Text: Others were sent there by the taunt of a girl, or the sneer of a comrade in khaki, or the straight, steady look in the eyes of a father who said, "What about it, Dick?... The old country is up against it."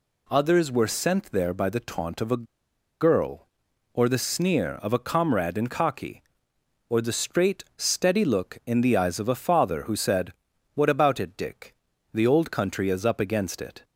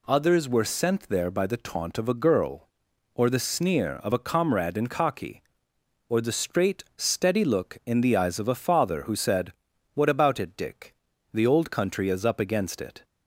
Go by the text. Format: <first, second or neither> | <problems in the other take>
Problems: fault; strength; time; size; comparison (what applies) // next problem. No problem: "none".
second | pauses between "a" and "girl"; noticeable; at 2.4 s; 0.57 s long